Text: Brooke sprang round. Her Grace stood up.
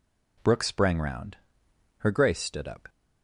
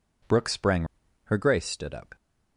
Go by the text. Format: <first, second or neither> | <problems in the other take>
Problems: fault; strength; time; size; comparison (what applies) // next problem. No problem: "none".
first | skips "round"; at 1.0 s